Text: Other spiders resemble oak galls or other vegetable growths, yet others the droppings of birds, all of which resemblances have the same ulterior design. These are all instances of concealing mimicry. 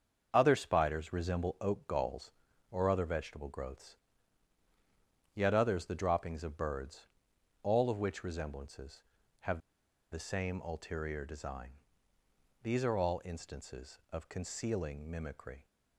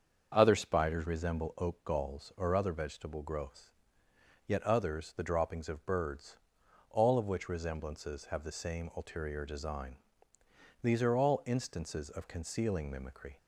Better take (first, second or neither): second